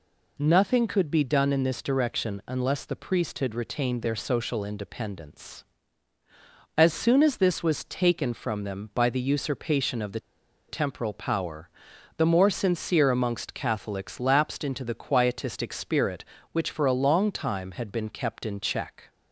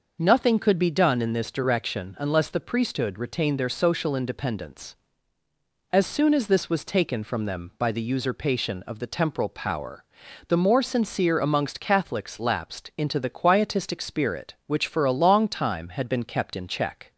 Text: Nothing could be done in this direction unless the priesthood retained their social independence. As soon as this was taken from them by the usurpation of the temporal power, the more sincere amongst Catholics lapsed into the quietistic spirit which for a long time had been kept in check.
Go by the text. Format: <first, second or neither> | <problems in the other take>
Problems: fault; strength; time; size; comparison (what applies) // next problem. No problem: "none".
second | pauses between "the" and "temporal"; noticeable; at 10.1 s; 0.49 s long